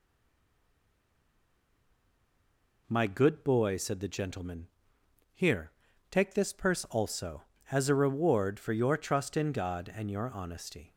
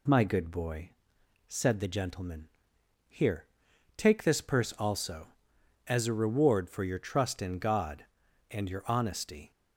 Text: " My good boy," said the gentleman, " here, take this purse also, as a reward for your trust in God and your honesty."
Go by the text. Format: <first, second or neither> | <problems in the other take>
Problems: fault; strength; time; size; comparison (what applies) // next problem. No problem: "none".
second | stays silent before the first word; strong; until 2.8 s; 2.8 s long